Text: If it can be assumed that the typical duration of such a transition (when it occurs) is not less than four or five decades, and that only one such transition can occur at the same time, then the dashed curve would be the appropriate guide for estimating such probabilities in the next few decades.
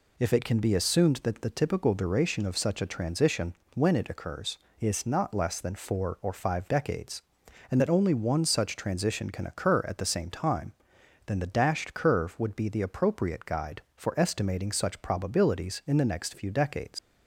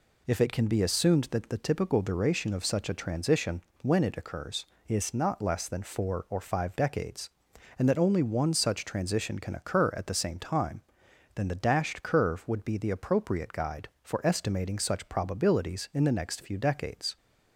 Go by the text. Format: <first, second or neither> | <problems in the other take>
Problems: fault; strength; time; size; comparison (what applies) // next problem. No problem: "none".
second | leaves "decades" unfinished; at 16.9 s; 105 ms